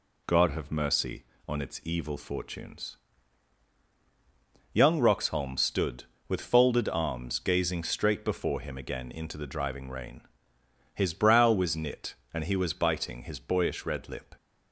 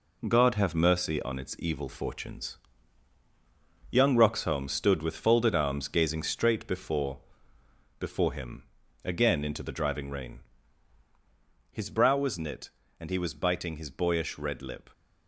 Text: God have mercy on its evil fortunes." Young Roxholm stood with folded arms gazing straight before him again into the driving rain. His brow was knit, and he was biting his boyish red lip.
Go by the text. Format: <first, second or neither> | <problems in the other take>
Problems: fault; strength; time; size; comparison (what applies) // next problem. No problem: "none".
first | says "before" twice; at 7.9 s // pauses between "him" and "again"; at 8.6 s; 0.40 s long